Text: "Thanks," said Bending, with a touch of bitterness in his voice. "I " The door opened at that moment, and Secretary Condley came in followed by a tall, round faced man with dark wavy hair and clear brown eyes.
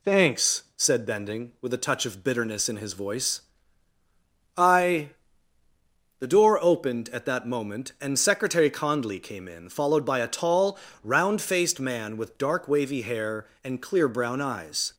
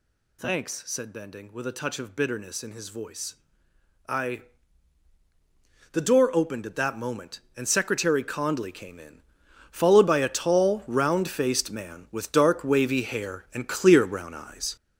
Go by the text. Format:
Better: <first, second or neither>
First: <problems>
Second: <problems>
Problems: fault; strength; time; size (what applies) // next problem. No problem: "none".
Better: first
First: none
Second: gets louder; strong; throughout; 11 dB // pauses between "in" and "followed"; noticeable; at 9.1 s; 0.50 s long